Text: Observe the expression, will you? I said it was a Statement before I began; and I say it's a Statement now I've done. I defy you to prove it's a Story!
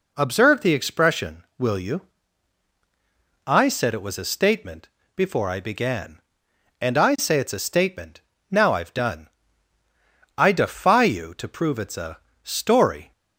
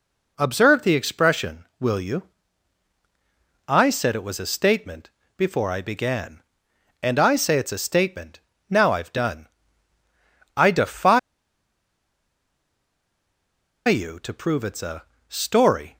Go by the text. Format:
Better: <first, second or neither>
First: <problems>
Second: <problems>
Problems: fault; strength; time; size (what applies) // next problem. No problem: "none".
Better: first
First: pauses between "Statement" and "before"; slight; at 4.8 s; 0.28 s long // pauses between "Statement" and "now"; slight; at 8.2 s; 0.28 s long // pauses between "a" and "Story"; slight; at 12.1 s; 0.24 s long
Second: pauses between "Statement" and "before"; slight; at 5.0 s; 0.28 s long // pauses between "Statement" and "now"; slight; at 8.4 s; 0.28 s long // pauses between "defy" and "you"; strong; at 11.1 s; 2.6 s long // pauses between "a" and "Story"; slight; at 15.0 s; 0.24 s long